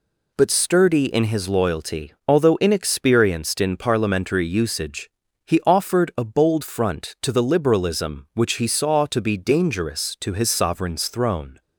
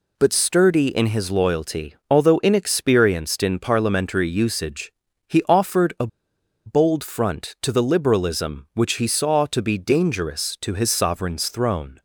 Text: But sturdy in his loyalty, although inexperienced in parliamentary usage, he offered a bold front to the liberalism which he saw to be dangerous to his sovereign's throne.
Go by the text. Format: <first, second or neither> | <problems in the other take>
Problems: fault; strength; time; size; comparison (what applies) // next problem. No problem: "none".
first | pauses between "a" and "bold"; noticeable; at 6.0 s; 0.58 s long